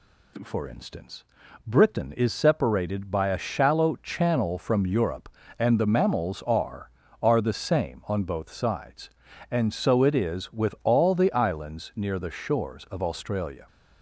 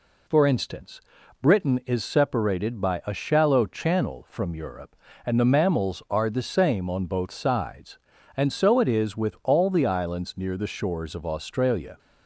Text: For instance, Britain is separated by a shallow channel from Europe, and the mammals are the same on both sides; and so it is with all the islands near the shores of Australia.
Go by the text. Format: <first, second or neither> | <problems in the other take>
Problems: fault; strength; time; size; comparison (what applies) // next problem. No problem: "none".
second | says "are" twice; at 7.2 s